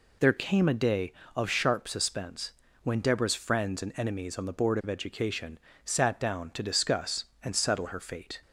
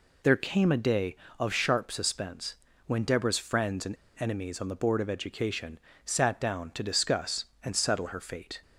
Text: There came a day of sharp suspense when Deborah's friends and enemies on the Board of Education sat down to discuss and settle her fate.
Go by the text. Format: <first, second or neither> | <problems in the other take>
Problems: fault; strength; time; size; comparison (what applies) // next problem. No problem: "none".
first | pauses between "suspense" and "when"; slight; at 2.5 s; 0.30 s long; slight in the first // pauses between "and" and "enemies"; slight; at 3.9 s; 0.25 s long // pauses between "Education" and "sat"; slight; at 5.7 s; 0.26 s long; slight in the first